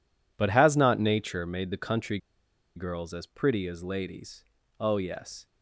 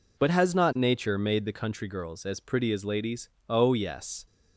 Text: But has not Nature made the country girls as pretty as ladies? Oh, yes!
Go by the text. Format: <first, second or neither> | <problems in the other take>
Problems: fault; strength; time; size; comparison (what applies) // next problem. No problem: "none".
second | pauses between "country" and "girls"; noticeable; at 2.1 s; 0.58 s long